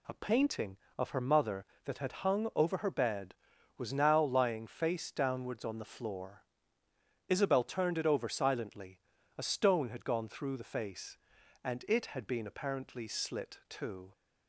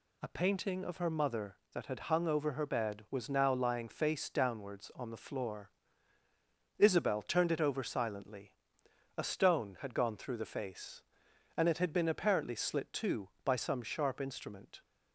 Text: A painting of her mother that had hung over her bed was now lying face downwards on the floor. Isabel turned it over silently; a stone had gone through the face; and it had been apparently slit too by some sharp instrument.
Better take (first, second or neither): second